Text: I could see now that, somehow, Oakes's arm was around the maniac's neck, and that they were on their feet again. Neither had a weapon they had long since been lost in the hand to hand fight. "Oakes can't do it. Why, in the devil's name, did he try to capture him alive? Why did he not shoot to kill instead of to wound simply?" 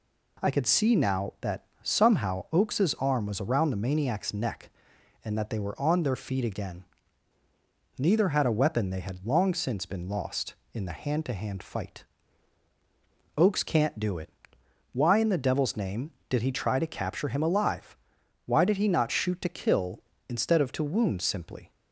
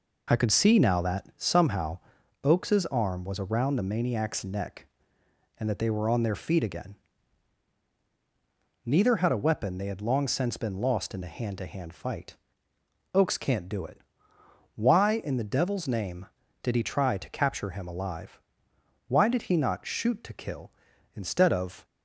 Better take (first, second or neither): first